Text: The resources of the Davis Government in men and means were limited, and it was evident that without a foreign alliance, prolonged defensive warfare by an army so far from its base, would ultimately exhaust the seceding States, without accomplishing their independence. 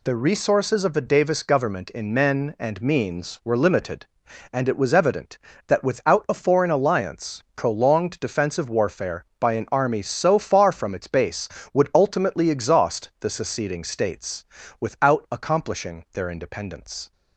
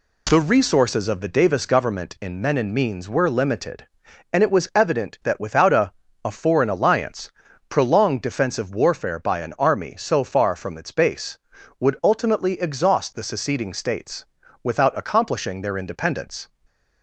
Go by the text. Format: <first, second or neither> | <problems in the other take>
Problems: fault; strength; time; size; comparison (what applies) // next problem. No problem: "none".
first | says "a" twice; at 6.2 s